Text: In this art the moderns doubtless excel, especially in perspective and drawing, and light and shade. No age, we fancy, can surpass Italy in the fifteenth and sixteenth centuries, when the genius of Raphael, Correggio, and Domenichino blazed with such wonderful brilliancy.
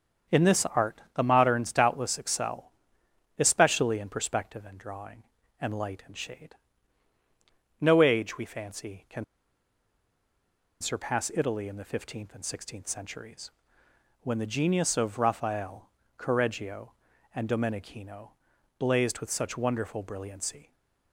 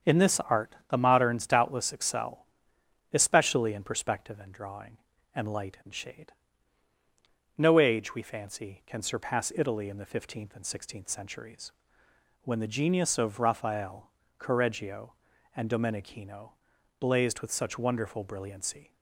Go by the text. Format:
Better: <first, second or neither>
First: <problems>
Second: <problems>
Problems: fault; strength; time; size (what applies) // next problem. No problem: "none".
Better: second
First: starts louder than the rest; strong; until 1.4 s; 7 dB // pauses between "can" and "surpass"; strong; at 9.2 s; 1.5 s long // pauses between "Domenichino" and "blazed"; noticeable; at 18.2 s; 0.48 s long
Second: starts louder than the rest; strong; until 1.1 s; 7 dB // pauses between "Domenichino" and "blazed"; noticeable; at 16.5 s; 0.48 s long